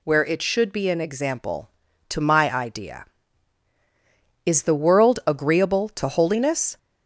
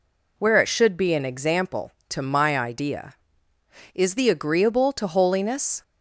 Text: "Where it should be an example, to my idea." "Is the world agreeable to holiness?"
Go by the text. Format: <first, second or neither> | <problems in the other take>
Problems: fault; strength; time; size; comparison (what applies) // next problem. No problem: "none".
first | skips "world"; at 4.2 s